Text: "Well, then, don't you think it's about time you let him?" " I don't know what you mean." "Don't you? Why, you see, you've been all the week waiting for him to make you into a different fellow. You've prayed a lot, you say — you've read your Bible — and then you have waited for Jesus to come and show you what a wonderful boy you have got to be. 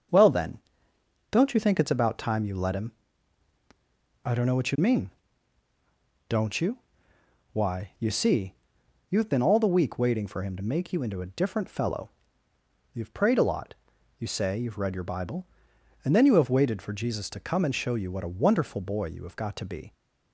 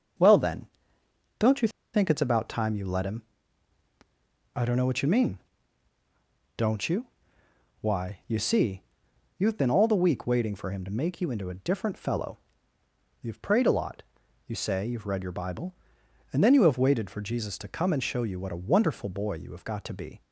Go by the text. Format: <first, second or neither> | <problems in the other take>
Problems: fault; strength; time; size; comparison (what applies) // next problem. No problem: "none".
first | starts louder than the rest; until 2.1 s; 7 dB; also in the first // pauses between "you" and "think"; slight; at 1.6 s; 0.25 s long